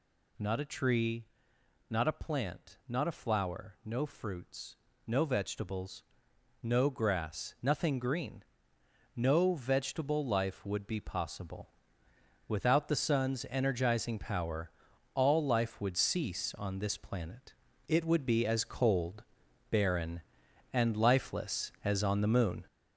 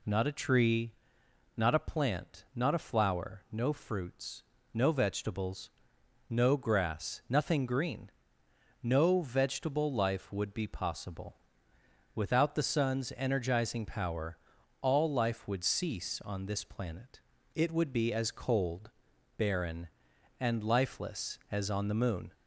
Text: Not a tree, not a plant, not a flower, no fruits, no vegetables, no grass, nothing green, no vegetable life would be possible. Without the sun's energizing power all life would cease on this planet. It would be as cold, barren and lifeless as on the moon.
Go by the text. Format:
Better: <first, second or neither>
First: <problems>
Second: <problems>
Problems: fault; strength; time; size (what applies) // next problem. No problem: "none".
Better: second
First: gets louder; noticeable; throughout; 5 dB // pauses between "power" and "all"; at 14.7 s; 0.44 s long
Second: pauses between "power" and "all"; at 14.3 s; 0.44 s long